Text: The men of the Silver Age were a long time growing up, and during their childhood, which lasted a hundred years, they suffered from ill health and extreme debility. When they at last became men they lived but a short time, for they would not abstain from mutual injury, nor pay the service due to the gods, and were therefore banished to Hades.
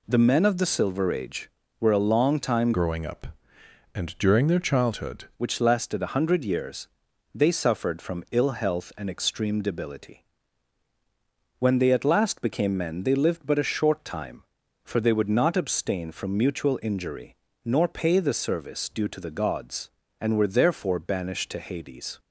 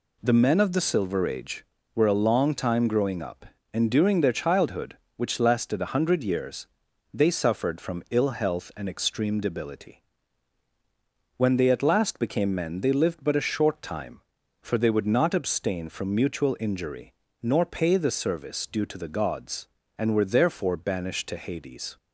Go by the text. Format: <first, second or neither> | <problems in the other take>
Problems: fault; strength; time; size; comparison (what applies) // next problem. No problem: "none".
second | changes voice from "growing" to "childhood"; from 2.7 to 5.2 s; 2.5 s long